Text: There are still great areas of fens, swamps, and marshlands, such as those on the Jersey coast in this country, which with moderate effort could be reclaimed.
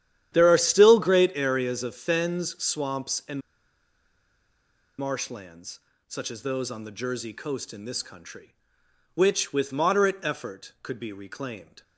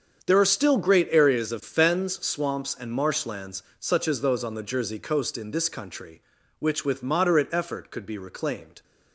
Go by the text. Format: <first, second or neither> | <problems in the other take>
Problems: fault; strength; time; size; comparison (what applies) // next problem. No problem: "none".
second | starts louder than the rest; strong; until 1.3 s; 10.5 dB; strong in the second // pauses between "and" and "marshlands"; strong; at 3.3 s; 1.5 s long